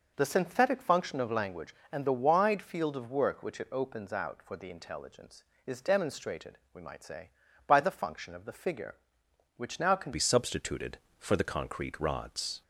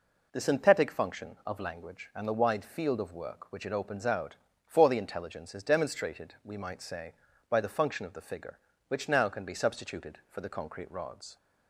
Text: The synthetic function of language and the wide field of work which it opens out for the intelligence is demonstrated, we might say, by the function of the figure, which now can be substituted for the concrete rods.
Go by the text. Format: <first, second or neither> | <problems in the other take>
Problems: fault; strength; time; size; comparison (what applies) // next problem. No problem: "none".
second | changes voice at "be"; from 10.1 s on; 2.5 s long